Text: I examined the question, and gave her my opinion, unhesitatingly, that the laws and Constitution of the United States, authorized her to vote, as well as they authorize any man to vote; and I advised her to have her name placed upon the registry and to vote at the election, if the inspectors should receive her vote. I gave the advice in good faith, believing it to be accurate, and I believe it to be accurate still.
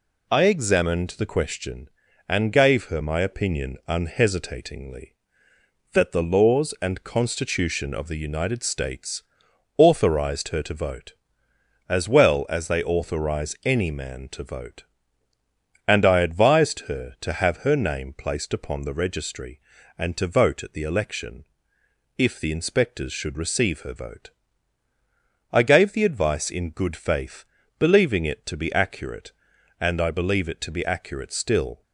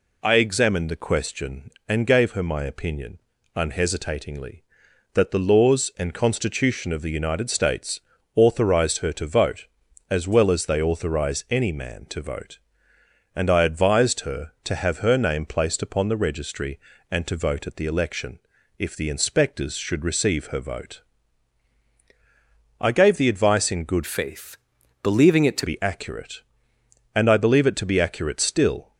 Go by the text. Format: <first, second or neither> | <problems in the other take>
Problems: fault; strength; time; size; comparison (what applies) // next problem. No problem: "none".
first | changes voice from "faith" to "to"; from 24.0 to 25.6 s; 1.6 s long